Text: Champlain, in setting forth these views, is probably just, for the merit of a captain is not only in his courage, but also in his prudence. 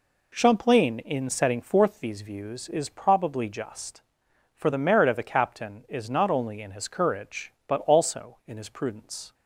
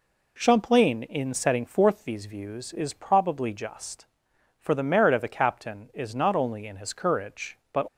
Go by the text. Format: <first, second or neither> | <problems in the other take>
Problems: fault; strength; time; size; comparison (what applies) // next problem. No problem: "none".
first | stops before "also in his prudence"; at 7.8 s